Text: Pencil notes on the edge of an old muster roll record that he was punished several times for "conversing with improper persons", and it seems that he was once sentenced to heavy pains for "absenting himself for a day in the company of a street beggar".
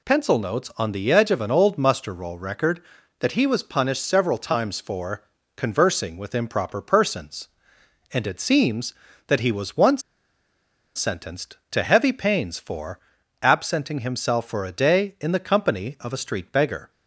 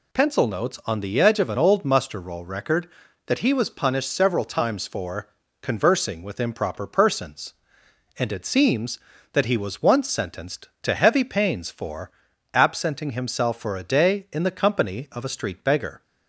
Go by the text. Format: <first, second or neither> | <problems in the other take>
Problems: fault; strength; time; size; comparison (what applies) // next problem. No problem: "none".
second | pauses between "for" and "conversing"; slight; at 5.2 s; 0.34 s long; slight in the second // pauses between "once" and "sentenced"; noticeable; at 10.0 s; 0.94 s long // pauses between "for" and "absenting"; at 13.0 s; 0.42 s long; also in the second